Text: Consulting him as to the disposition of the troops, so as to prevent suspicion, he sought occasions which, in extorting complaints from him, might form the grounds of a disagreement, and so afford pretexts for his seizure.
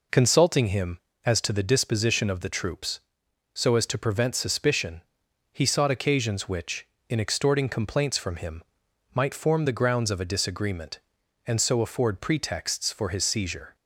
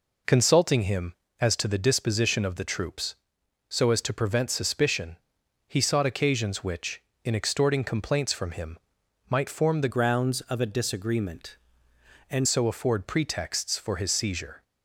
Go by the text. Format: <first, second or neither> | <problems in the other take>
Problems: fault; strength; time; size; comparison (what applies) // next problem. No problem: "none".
first | changes voice from "grounds" to "and"; from 9.8 to 12.4 s; 2.6 s long